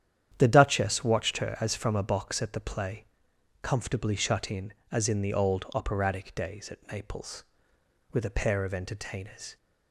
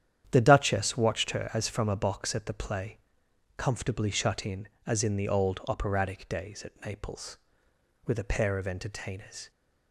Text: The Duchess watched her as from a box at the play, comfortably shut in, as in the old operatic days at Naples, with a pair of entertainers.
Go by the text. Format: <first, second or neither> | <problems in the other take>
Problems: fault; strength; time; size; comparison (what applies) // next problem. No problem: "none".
neither | starts louder than the rest; strong; the same in both